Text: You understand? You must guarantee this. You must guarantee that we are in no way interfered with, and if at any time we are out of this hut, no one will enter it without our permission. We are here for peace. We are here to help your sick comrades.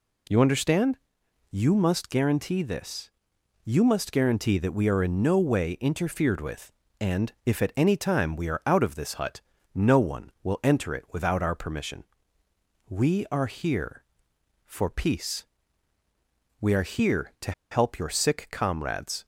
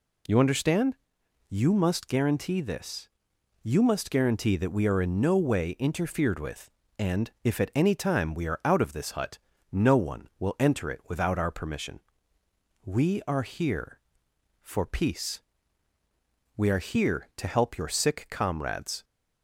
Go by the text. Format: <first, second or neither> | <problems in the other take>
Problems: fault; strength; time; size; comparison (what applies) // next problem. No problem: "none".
second | pauses between "to" and "help"; slight; at 17.5 s; 0.19 s long